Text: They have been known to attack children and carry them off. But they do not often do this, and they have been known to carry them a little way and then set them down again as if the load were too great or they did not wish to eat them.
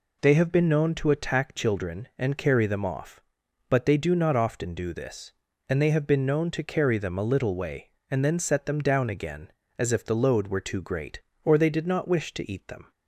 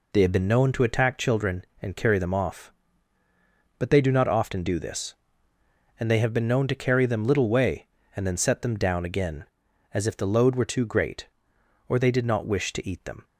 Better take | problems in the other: first | skips "a"; at 7.2 s

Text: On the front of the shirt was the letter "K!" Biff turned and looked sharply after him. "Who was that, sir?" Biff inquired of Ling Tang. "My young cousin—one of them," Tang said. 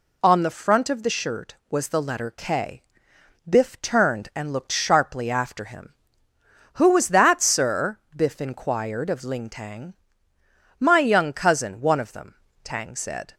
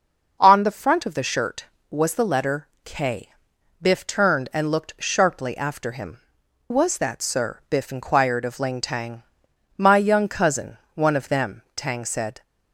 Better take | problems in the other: first | pauses between "letter" and "K"; slight; at 2.6 s; 0.16 s long // skips "Who"; at 6.4 s

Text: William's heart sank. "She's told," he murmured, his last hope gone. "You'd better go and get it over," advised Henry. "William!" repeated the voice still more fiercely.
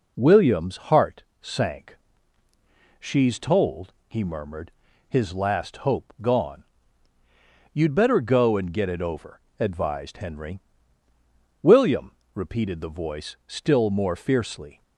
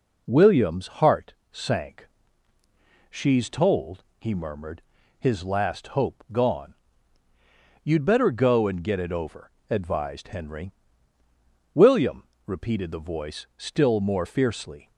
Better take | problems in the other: neither | pauses between "heart" and "sank"; slight; the same in both

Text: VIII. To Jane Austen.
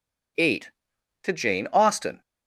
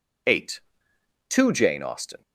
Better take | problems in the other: neither | none

